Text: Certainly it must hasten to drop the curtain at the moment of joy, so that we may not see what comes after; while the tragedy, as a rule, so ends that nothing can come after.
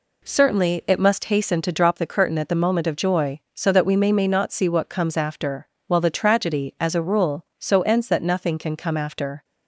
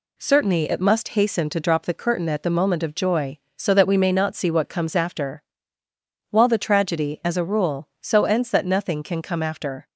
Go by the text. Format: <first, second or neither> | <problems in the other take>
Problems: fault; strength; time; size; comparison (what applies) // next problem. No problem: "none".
second | says "may" twice; at 4.1 s